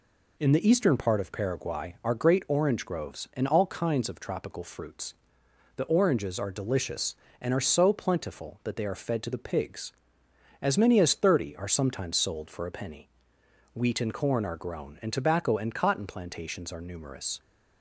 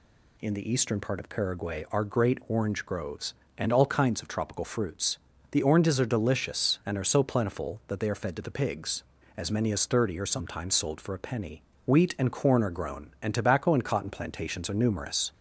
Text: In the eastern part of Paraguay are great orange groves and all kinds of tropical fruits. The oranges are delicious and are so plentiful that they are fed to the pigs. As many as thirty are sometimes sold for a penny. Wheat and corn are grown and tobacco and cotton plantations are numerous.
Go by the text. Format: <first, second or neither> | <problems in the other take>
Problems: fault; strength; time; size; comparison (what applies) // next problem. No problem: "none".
neither | none